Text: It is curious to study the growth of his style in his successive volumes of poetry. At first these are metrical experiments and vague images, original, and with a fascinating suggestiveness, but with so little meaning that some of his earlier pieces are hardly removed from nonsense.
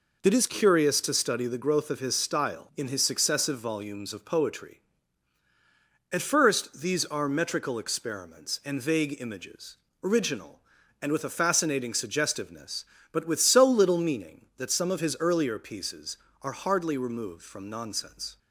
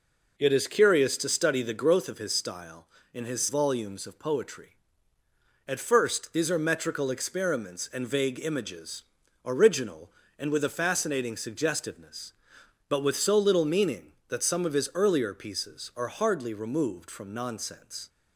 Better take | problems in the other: first | skips "successive"; at 3.4 s

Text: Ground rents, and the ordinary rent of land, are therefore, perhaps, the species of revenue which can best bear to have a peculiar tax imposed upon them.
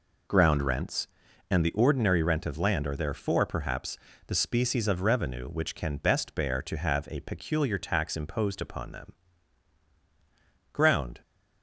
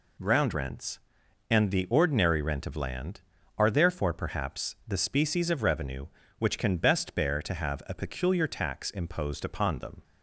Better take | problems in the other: second | goes on to say "Ground"; slight; from 10.7 s on; 0.48 s long

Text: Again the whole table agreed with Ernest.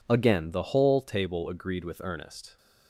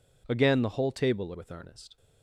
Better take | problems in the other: first | skips "agreed"; at 1.3 s

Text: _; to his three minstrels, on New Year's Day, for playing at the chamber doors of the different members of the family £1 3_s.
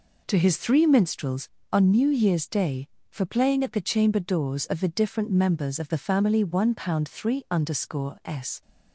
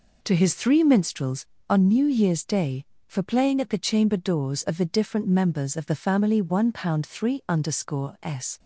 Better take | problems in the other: neither | none

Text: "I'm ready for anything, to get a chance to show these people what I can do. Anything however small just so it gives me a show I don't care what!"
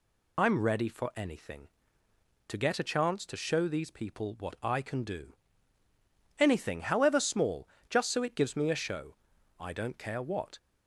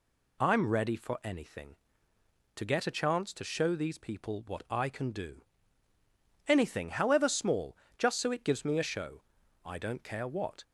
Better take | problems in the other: second | loses the start of "I'm"; at 0.3 s; 55 ms // pauses between "small" and "just"; slight; at 7.6 s; 0.22 s long; slight in the second // pauses between "show" and "I"; at 9.1 s; 0.44 s long; also in the second

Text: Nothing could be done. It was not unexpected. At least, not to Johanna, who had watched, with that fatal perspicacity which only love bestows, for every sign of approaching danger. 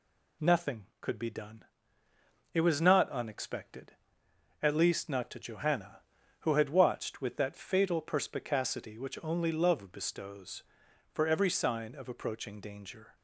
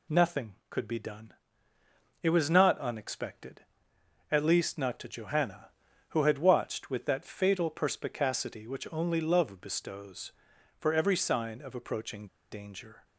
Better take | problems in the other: first | pauses between "approaching" and "danger"; slight; at 12.2 s; 0.25 s long

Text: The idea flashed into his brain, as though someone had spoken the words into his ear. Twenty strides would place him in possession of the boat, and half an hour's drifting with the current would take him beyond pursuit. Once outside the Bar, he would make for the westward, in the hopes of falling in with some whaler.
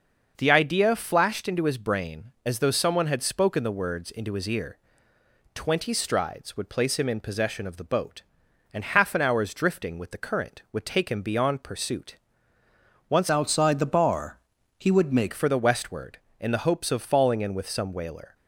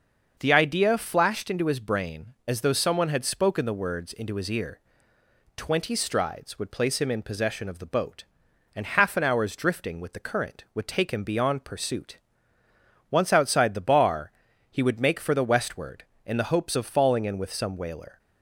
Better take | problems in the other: second | starts louder than the rest; until 1.3 s; 6 dB; also in the second // changes voice from "outside" to "make"; from 13.2 to 15.3 s; 2.1 s long

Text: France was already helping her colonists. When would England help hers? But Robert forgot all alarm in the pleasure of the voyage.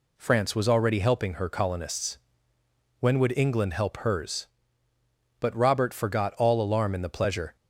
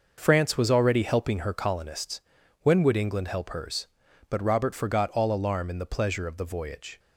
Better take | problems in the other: second | stops before "of the voyage"; at 7.5 s

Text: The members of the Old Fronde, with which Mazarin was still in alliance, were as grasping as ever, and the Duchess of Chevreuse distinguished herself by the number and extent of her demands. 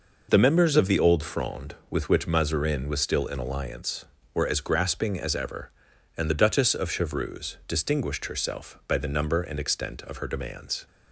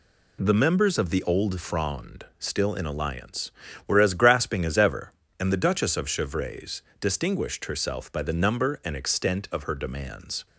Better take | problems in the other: first | skips "with which Mazarin was"; at 2.3 s // pauses between "Chevreuse" and "distinguished"; slight; at 6.8 s; 0.20 s long

